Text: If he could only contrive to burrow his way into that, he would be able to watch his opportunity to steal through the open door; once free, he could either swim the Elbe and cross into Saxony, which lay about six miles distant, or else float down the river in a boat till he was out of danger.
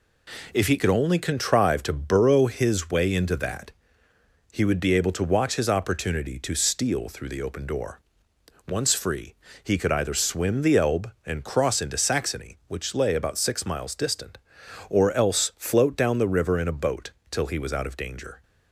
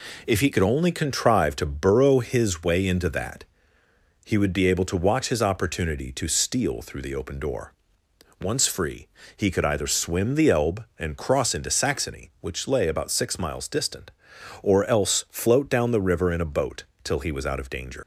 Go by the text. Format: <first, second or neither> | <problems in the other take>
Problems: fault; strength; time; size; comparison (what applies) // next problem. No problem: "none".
first | pauses between "boat" and "till"; slight; at 16.8 s; 0.18 s long; slight in the first // leaves "danger" unfinished; at 18.0 s; 120 ms